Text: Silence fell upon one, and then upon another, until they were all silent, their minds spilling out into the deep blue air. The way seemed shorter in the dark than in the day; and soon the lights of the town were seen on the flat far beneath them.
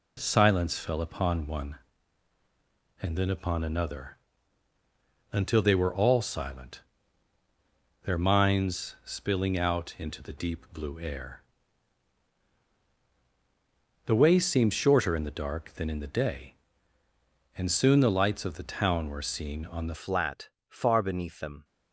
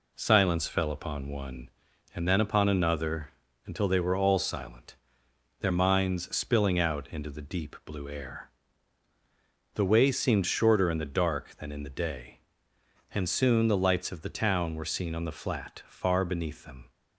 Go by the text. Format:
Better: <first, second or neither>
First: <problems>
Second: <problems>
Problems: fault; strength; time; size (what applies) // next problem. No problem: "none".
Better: second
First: changes voice at "flat"; from 19.9 s on; 1.7 s long // pauses between "flat" and "far"; slight; at 20.5 s; 0.18 s long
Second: none